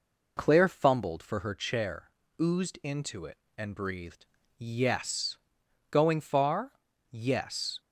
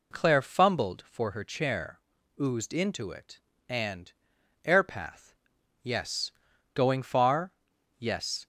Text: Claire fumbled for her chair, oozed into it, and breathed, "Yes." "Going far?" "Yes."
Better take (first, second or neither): first